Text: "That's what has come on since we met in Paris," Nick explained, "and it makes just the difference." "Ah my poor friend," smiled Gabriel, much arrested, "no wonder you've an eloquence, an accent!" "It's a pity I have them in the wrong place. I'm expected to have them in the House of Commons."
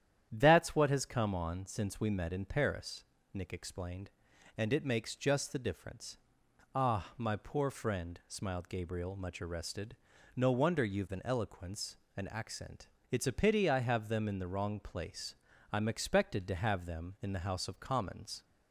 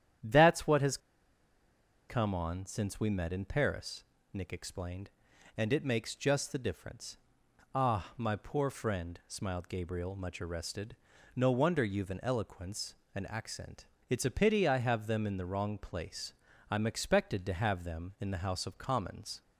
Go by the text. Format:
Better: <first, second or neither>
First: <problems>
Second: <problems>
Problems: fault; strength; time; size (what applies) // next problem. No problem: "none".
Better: first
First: starts louder than the rest; strong; until 1.3 s; 10 dB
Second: starts louder than the rest; strong; until 2.3 s; 10 dB // pauses between "has" and "come"; at 0.9 s; 1.1 s long